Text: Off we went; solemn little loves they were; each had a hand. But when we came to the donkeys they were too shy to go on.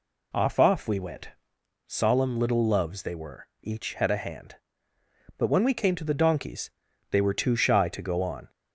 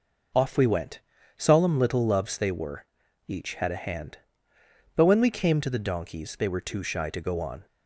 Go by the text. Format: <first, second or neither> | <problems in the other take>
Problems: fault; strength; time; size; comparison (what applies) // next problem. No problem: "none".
second | says "Off" twice; at 0.5 s // pauses between "donkeys" and "they"; at 6.6 s; 0.40 s long